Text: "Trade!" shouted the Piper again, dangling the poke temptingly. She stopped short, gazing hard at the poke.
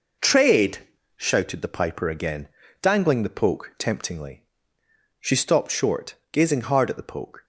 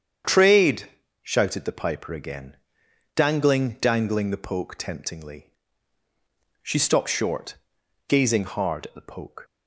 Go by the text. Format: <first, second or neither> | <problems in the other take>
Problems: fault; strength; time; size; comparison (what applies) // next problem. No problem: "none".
first | starts louder than the rest; strong; until 1.5 s; 8 dB // says "dangling" twice; at 3.7 s